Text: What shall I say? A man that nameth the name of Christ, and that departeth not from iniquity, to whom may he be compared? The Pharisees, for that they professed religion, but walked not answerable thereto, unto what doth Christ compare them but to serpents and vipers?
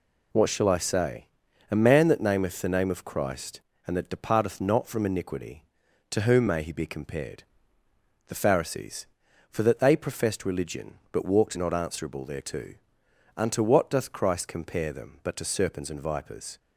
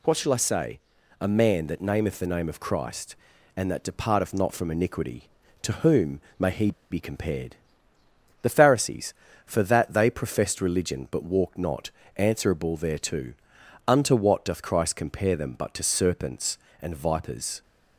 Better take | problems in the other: first | pauses between "whom" and "may"; slight; at 6.2 s; 0.18 s long // pauses between "he" and "be"; slight; at 6.7 s; 0.19 s long // pauses between "not" and "answerable"; slight; at 11.9 s; 0.24 s long

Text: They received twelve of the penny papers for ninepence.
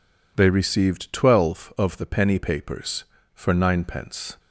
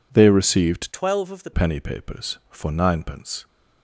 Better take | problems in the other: first | changes voice from "twelve" to "the"; from 0.9 to 1.5 s; 0.6 s long

